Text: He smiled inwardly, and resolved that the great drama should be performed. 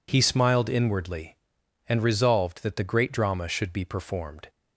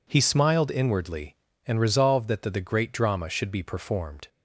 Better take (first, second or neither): first